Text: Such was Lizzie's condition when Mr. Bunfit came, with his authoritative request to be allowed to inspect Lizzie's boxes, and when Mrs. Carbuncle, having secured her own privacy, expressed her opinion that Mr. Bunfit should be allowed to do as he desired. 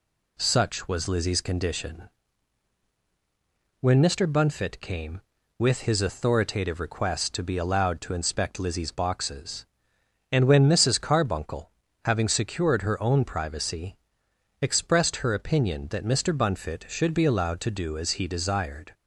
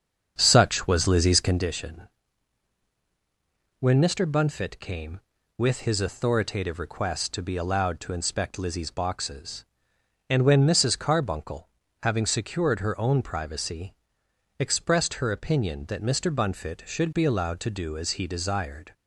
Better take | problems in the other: first | starts louder than the rest; until 1.7 s; 7 dB // pauses between "condition" and "when"; strong; at 2.0 s; 1.7 s long; strong in the first

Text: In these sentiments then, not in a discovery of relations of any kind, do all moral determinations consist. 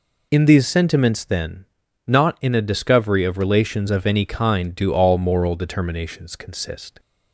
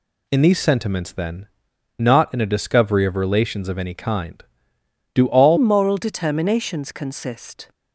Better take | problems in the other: first | changes voice at "moral"; from 5.5 s on; 2.2 s long

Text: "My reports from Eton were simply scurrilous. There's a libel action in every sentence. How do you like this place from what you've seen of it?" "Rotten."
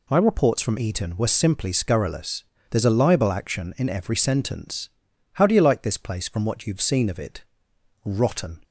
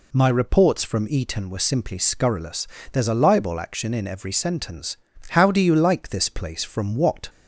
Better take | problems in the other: first | stops before "you've seen of it Rotten"; at 7.2 s

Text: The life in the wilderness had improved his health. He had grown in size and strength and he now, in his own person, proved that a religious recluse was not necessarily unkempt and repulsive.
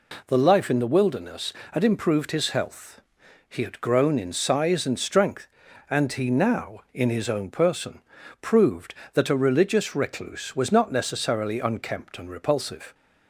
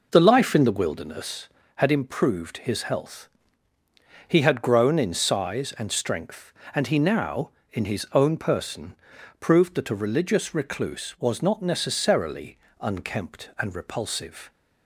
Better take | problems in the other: first | starts louder than the rest; noticeable; until 1.9 s; 5 dB // pauses between "necessarily" and "unkempt"; slight; at 12.5 s; 0.22 s long

